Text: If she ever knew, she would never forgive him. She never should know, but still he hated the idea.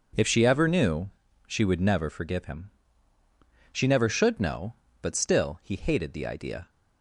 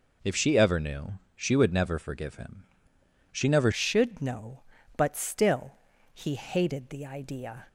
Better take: first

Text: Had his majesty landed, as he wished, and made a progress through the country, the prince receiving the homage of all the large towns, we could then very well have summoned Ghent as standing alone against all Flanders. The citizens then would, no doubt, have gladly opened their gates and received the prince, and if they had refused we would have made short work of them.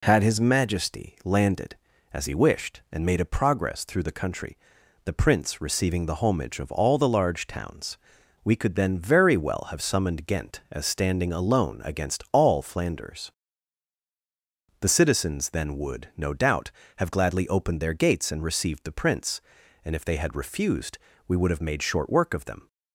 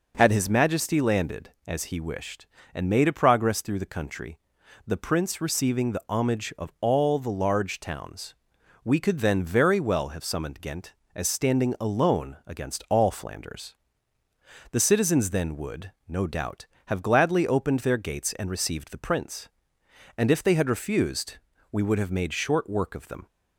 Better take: neither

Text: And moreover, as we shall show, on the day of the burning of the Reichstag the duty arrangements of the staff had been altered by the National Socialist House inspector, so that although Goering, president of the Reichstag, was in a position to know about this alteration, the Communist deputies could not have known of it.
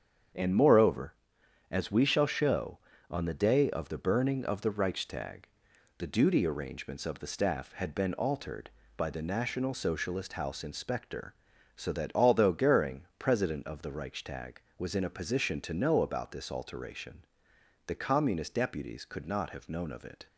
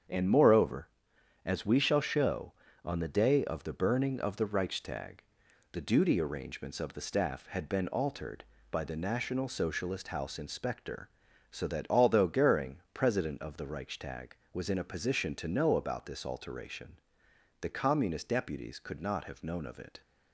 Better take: neither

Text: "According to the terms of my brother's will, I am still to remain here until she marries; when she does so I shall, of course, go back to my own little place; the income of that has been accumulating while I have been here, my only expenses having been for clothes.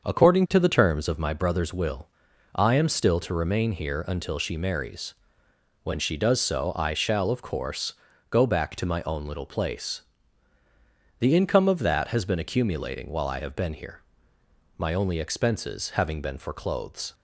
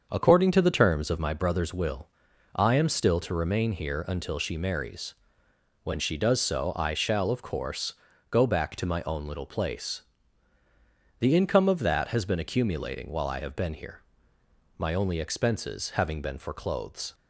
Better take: neither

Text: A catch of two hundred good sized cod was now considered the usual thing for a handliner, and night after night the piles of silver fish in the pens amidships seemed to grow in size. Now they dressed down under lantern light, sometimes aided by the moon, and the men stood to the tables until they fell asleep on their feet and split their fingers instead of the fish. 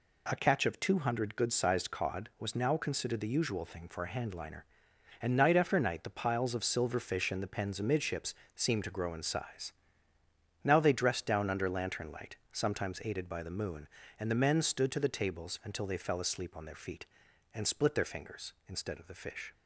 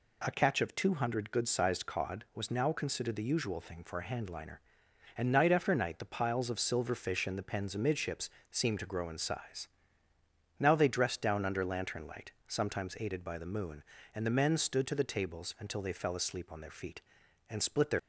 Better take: first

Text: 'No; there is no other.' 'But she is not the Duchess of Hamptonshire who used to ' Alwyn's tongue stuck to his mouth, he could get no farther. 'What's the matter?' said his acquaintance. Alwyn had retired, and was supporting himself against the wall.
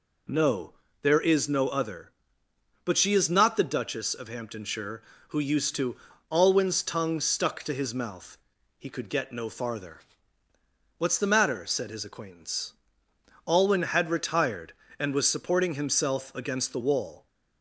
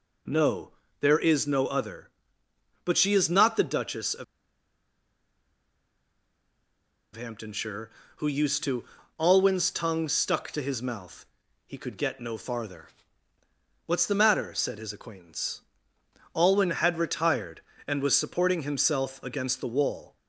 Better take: first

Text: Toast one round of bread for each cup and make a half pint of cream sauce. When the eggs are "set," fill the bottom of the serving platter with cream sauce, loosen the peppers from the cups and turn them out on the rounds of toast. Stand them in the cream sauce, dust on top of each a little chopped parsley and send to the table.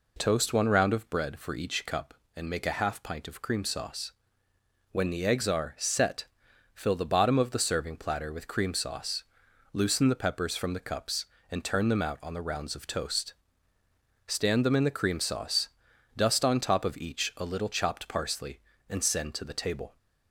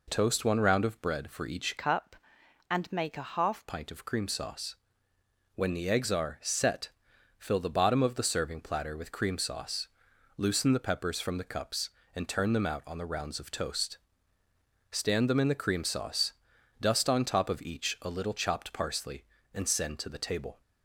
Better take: first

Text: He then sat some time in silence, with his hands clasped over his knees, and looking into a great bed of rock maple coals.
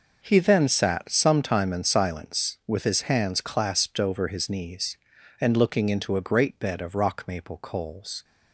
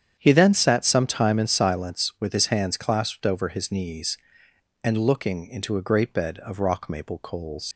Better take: first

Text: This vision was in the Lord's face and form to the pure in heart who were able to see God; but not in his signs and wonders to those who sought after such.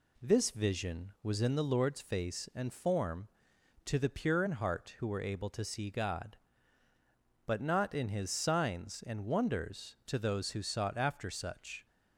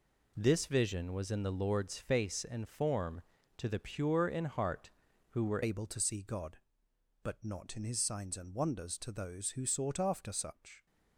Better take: first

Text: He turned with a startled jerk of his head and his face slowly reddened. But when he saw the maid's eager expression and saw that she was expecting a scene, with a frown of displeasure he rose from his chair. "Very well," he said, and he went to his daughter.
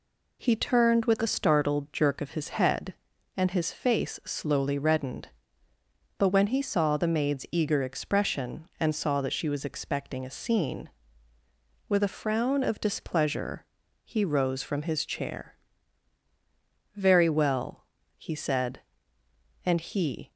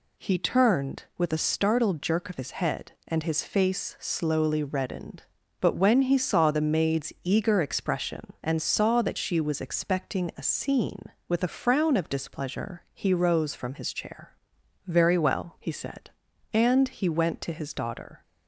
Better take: second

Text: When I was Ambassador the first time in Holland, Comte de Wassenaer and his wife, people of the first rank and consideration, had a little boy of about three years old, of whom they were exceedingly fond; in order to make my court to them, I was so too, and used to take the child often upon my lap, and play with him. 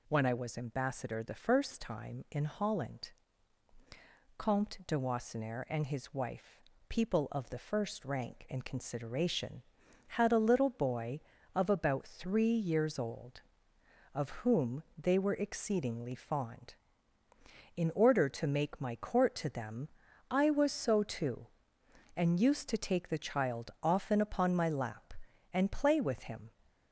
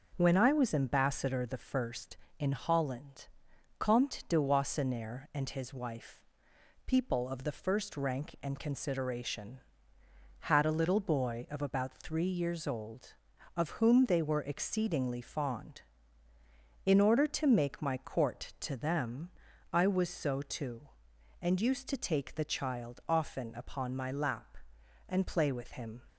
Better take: first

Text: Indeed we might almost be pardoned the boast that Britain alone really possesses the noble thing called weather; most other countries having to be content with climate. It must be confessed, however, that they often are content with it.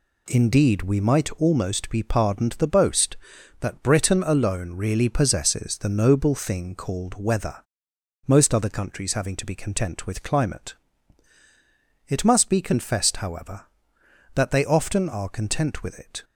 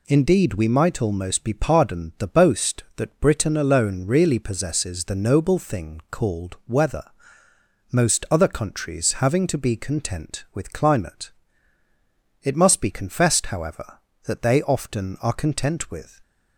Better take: first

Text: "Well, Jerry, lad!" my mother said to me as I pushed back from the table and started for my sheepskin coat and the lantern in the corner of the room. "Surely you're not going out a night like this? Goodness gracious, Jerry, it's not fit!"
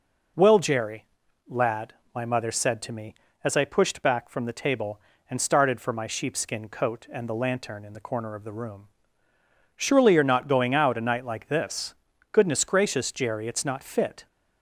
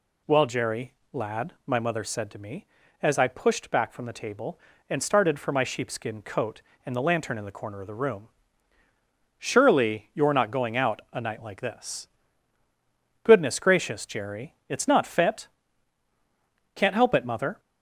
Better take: first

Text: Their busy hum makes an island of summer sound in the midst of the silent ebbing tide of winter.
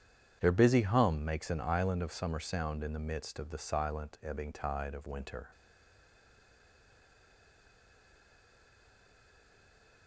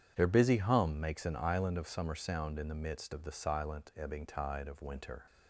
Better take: second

